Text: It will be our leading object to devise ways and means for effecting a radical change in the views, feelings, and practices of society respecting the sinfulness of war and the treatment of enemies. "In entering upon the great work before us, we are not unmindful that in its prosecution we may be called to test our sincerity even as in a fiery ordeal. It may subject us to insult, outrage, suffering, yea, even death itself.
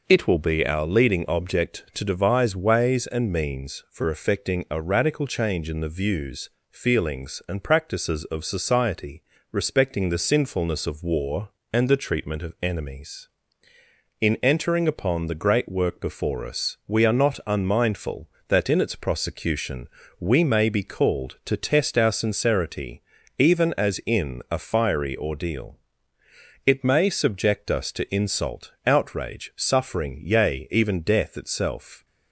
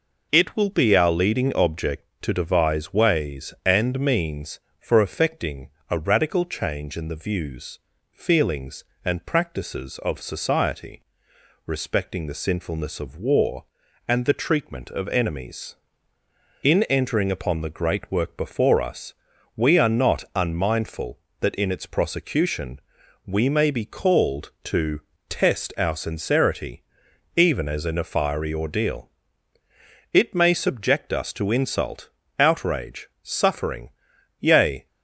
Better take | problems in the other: first | pauses between "effecting" and "a"; slight; at 5.6 s; 0.20 s long // pauses between "society" and "respecting"; noticeable; at 11.0 s; 0.62 s long; slight in the first // pauses between "prosecution" and "we"; noticeable; at 22.7 s; 0.46 s long; slight in the first // pauses between "to" and "test"; slight; at 25.0 s; 0.26 s long // pauses between "sincerity" and "even"; noticeable; at 26.8 s; 0.52 s long; also in the first // stops before "even death itself"; at 34.8 s

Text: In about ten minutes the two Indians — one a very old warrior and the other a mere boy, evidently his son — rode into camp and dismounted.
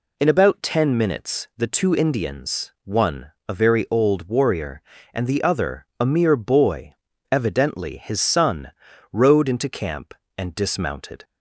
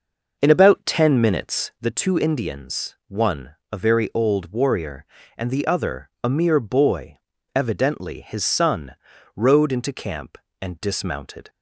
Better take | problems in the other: first | starts louder than the rest; noticeable; until 1.9 s; 6 dB // pauses between "one" and "a"; slight; at 3.5 s; 0.16 s long; slight in the first

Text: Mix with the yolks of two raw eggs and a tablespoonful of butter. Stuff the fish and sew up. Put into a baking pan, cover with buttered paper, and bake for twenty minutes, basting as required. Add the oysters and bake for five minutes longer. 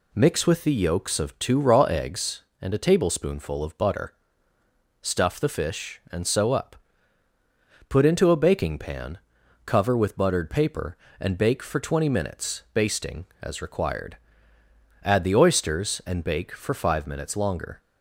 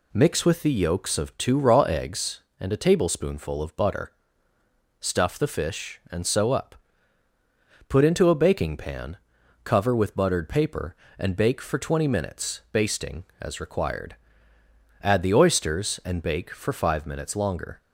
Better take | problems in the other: neither | none

